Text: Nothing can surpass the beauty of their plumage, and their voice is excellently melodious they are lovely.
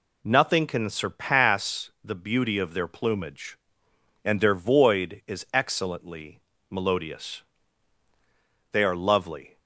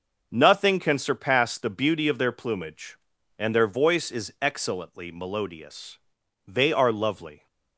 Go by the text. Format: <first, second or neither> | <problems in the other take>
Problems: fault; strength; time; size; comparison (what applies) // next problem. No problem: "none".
second | says "void" for "voice"; at 4.5 s // pauses between "excellently" and "melodious"; slight; at 6.3 s; 0.30 s long // pauses between "melodious" and "they"; strong; at 7.4 s; 1.3 s long; noticeable in the second